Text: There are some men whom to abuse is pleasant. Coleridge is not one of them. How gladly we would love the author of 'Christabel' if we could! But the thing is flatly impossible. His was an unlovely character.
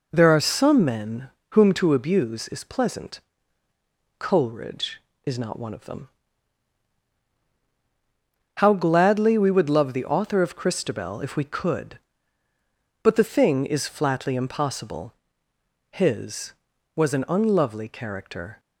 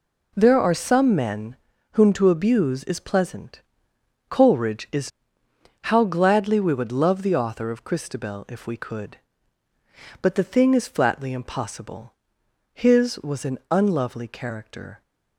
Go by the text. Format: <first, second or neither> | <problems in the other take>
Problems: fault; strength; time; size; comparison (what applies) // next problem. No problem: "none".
first | pauses between "men" and "whom"; slight; at 1.5 s; 0.36 s long; slight in the first // skips "not one of them"; at 5.4 s